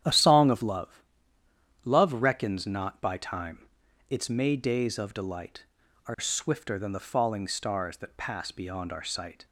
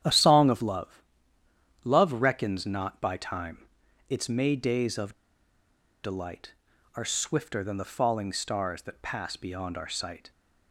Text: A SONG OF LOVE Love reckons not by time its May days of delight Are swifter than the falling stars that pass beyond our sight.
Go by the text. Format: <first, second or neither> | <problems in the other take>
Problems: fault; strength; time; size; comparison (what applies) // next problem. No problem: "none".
first | starts louder than the rest; strong; until 1.8 s; 10 dB; strong in the first // pauses between "LOVE" and "Love"; noticeable; at 1.0 s; 0.82 s long; noticeable in the first // pauses between "time" and "its"; at 3.6 s; 0.42 s long; also in the first // pauses between "of" and "delight"; noticeable; at 5.1 s; 0.89 s long